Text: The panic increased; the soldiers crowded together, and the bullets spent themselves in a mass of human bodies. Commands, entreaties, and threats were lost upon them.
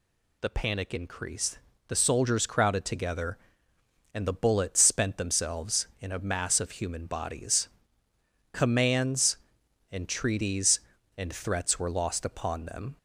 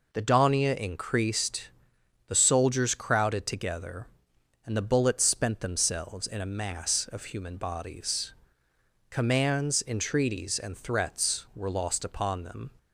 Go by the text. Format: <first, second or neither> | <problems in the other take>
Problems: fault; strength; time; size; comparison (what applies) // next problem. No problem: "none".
first | says "donia" for "panic"; at 0.2 s